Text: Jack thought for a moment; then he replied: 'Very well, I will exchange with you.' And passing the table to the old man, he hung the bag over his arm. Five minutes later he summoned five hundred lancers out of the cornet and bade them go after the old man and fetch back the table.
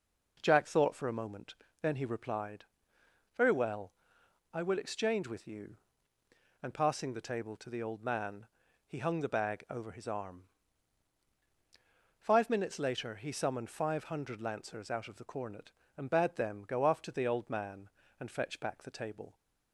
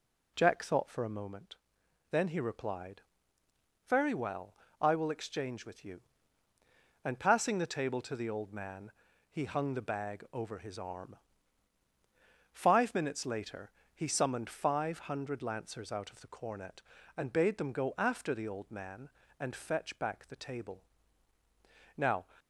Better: first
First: none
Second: pauses between "later" and "he"; slight; at 13.7 s; 0.22 s long // goes on to say "Now"; slight; from 21.9 s on; 0.26 s long

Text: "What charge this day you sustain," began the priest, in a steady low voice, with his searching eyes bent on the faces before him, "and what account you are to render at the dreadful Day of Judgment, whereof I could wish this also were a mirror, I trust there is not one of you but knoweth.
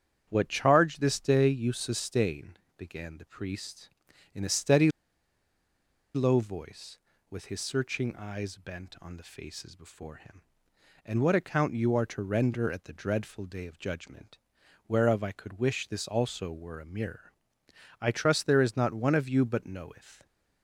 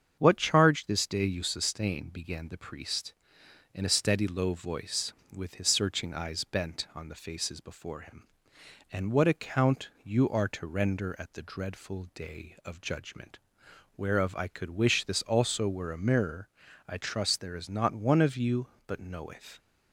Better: second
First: starts louder than the rest; strong; until 1.3 s; 9 dB // pauses between "steady" and "low"; strong; at 4.8 s; 1.2 s long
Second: starts louder than the rest; strong; until 1.1 s; 7.5 dB

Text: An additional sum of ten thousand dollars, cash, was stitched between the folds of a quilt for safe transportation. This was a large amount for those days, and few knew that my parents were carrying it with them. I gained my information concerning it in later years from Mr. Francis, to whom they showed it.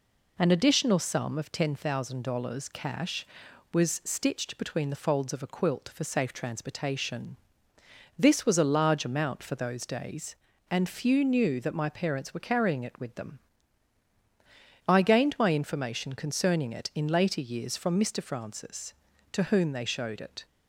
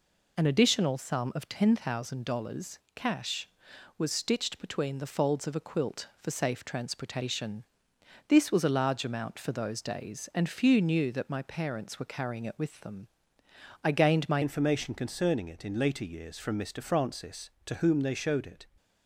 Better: first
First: none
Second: changes voice at "information"; from 14.4 s on; 4.2 s long

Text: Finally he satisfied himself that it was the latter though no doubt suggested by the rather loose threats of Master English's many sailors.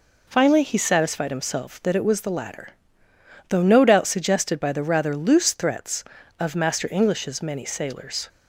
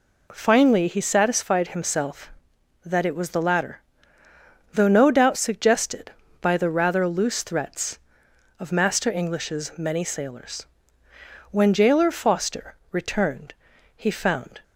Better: first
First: pauses between "latter" and "though"; noticeable; at 2.6 s; 0.82 s long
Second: pauses between "latter" and "though"; noticeable; at 3.7 s; 0.94 s long // goes on to say "When jailer Foster returned he found"; strong; from 11.5 s on; 3.1 s long

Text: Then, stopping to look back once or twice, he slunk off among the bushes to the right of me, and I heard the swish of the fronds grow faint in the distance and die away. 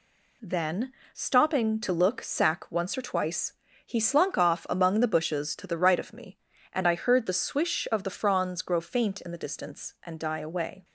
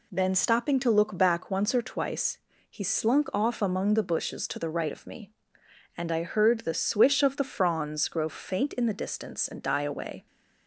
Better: second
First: says "sack" for "back"; at 2.2 s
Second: none

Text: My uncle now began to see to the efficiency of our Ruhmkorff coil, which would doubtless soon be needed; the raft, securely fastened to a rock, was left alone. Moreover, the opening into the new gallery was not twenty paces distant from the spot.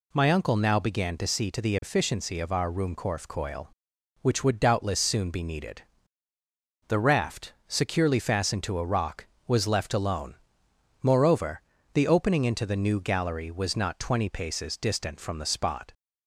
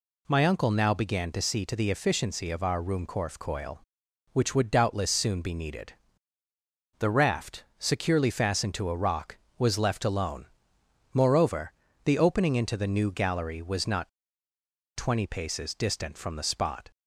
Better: first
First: none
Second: pauses between "not" and "twenty"; noticeable; at 14.0 s; 0.87 s long

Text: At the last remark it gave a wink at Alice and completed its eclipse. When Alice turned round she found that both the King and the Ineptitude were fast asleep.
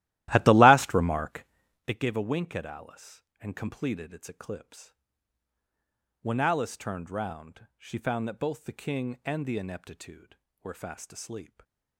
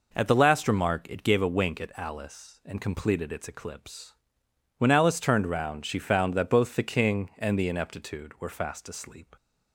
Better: second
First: starts louder than the rest; strong; until 1.9 s; 15 dB // pauses between "remark" and "it"; at 1.4 s; 0.44 s long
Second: none

